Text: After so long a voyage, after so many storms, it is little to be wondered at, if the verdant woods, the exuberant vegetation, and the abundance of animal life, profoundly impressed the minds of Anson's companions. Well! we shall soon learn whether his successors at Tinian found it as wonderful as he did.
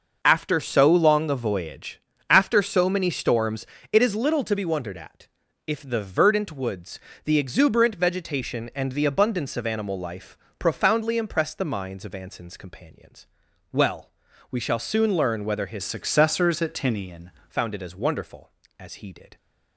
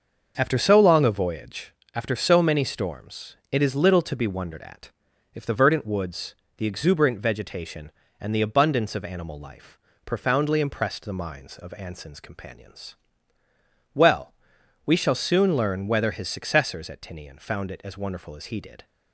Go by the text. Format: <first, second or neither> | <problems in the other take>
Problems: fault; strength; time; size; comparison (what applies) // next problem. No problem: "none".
second | starts louder than the rest; noticeable; until 1.2 s; 6 dB; also in the second // changes voice from "successors" to "Tinian"; from 15.8 to 17.3 s; 1.5 s long